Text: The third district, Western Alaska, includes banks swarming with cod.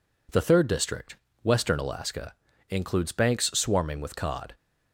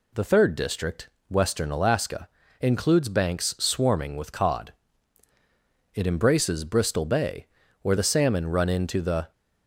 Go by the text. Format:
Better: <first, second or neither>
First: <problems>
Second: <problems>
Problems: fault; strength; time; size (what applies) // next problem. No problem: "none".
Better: first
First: none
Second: goes on to say "It embraces Bristol Bay where the salmon run into the"; strong; from 5.9 s on; 3.3 s long